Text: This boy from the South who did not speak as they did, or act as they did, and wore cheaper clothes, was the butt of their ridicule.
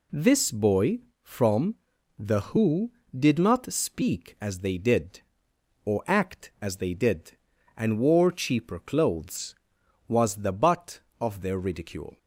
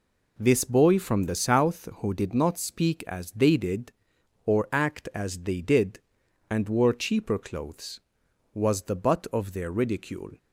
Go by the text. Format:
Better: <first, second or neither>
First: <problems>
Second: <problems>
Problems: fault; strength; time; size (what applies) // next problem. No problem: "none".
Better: second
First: pauses between "from" and "the"; at 1.7 s; 0.44 s long // skips "South"; at 2.3 s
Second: none